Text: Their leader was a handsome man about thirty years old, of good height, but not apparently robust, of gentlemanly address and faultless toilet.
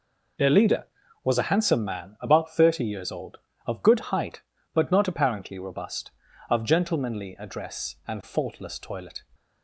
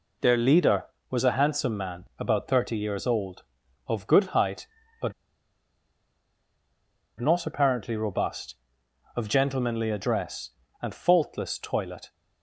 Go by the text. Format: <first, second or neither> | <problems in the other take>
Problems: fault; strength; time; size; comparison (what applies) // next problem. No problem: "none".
first | pauses between "but" and "not"; strong; at 5.1 s; 2.0 s long